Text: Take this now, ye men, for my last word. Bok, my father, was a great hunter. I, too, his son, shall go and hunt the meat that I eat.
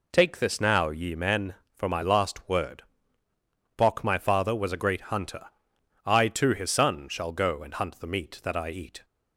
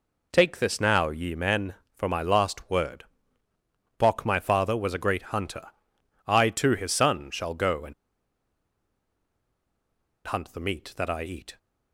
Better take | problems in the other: first | pauses between "and" and "hunt"; strong; at 7.9 s; 2.3 s long

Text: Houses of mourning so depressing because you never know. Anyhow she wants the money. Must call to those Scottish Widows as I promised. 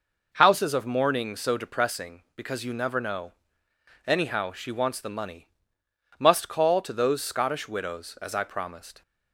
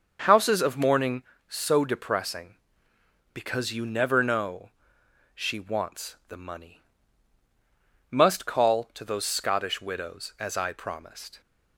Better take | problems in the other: first | starts louder than the rest; until 1.5 s; 6.5 dB // skips "Anyhow"; at 5.0 s

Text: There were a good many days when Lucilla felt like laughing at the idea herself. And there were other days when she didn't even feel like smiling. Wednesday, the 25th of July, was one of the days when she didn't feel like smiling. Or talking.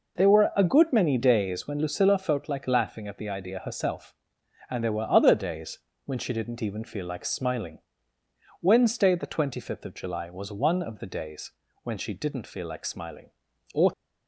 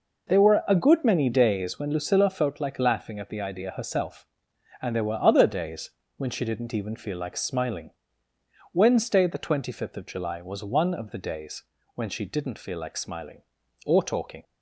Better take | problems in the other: second | pauses between "days" and "when"; slight; at 5.7 s; 0.26 s long; slight in the second // pauses between "days" and "when"; slight; at 11.5 s; 0.32 s long; slight in the second // stops before "talking"; at 13.9 s

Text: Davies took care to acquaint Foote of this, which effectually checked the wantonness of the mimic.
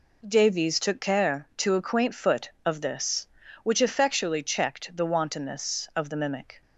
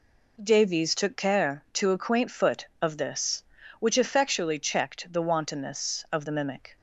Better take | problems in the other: neither | none

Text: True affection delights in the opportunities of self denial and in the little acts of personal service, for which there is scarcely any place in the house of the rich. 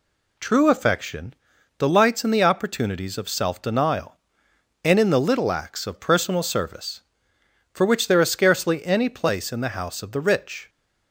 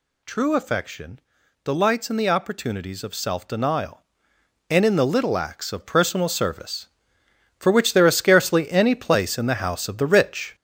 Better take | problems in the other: first | gets louder; throughout; 6 dB // pauses between "affection" and "delights"; at 1.1 s; 0.44 s long; also in the first

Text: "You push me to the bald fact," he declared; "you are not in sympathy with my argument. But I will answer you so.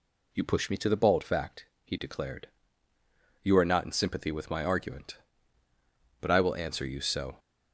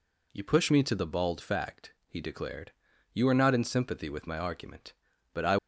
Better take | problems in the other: first | stops before "will answer you so"; at 5.5 s

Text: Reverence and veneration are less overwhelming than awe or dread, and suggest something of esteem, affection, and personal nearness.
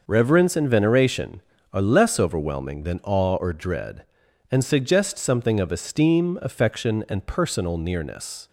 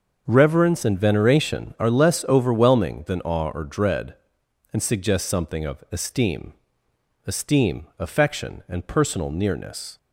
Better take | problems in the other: first | starts louder than the rest; until 1.2 s; 6.5 dB // says "esteem" twice; at 7.2 s

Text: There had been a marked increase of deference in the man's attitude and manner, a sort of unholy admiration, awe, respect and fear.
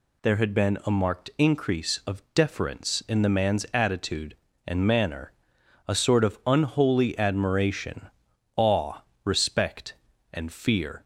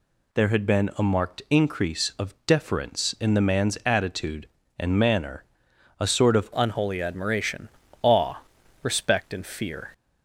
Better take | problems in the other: first | changes voice at "unholy"; from 6.5 s on; 3.3 s long

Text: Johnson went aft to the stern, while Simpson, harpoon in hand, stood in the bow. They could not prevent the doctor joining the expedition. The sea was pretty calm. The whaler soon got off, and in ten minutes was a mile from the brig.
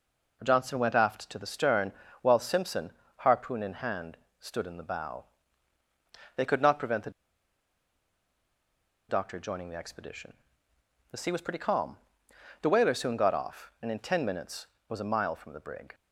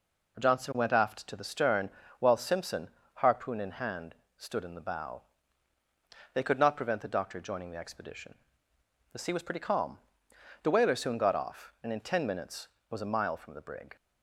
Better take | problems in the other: second | pauses between "the" and "doctor"; strong; at 7.0 s; 1.9 s long

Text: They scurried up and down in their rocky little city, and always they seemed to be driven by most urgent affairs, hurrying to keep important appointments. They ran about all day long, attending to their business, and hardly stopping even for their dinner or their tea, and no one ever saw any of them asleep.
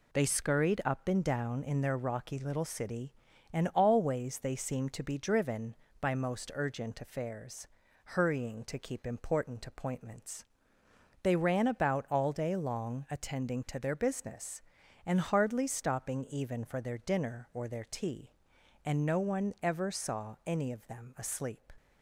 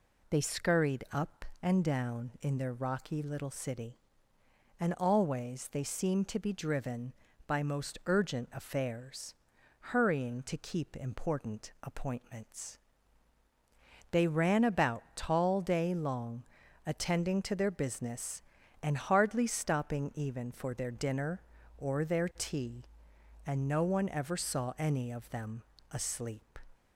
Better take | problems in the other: first | says "tall" for "all"; at 15.1 s // pauses between "them" and "asleep"; slight; at 25.6 s; 0.28 s long

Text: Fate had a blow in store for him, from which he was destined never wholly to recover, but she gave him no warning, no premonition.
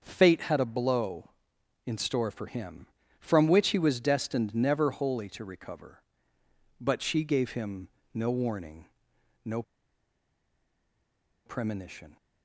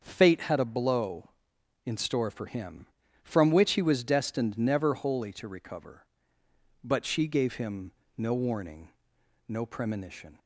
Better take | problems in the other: second | starts louder than the rest; until 1.0 s; 6.5 dB; also in the second // pauses between "him" and "no"; slight; at 7.8 s; 0.26 s long; slight in the second // pauses between "no" and "premonition"; strong; at 9.6 s; 1.8 s long

